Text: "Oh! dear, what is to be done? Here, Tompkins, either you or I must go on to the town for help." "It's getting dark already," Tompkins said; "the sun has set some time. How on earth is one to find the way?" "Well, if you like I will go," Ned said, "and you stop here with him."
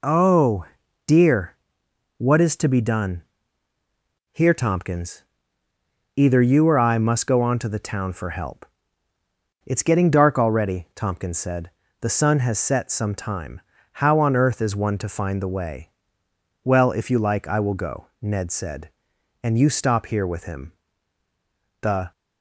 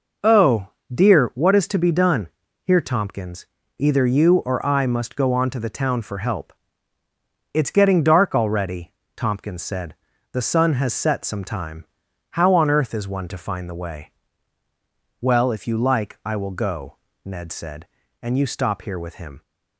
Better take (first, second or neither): second